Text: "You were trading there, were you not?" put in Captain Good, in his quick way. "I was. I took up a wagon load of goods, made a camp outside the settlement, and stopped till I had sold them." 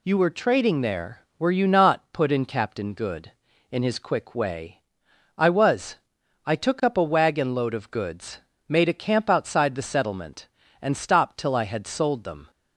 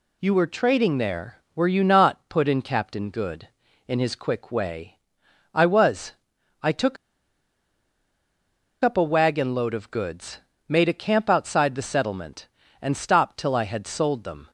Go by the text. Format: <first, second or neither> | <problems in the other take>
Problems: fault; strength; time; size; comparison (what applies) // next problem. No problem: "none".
first | pauses between "took" and "up"; strong; at 6.9 s; 1.8 s long